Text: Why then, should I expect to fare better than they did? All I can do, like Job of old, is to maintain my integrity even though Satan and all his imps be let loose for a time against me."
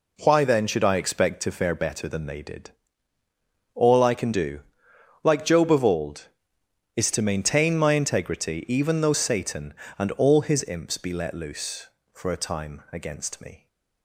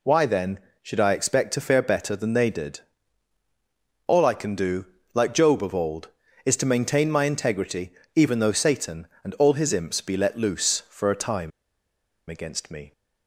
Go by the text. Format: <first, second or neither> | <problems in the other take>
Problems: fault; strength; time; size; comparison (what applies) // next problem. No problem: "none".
first | pauses between "integrity" and "even"; slight; at 7.9 s; 0.24 s long // pauses between "time" and "against"; noticeable; at 11.5 s; 0.79 s long